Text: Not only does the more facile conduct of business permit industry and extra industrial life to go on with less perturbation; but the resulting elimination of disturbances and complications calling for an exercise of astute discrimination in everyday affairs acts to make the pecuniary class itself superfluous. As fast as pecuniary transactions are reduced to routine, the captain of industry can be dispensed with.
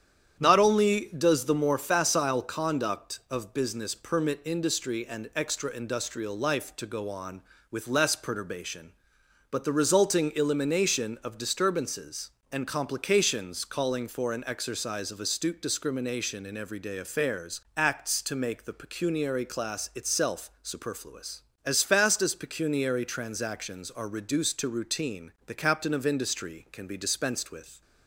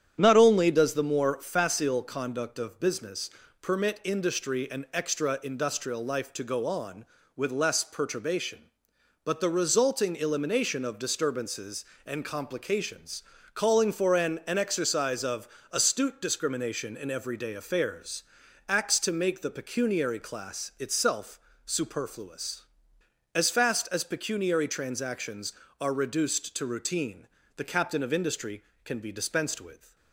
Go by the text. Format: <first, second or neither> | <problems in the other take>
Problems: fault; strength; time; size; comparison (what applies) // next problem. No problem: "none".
first | starts louder than the rest; strong; until 1.2 s; 9 dB; strong in the first // pauses between "business" and "permit"; slight; at 3.2 s; 0.32 s long // pauses between "complications" and "calling"; slight; at 13.2 s; 0.32 s long // says "an" twice; at 14.4 s // pauses between "of" and "astute"; slight; at 15.4 s; 0.24 s long // pauses between "affairs" and "acts"; at 18.2 s; 0.44 s long; slight in the first // pauses between "itself" and "superfluous"; slight; at 21.3 s; 0.26 s long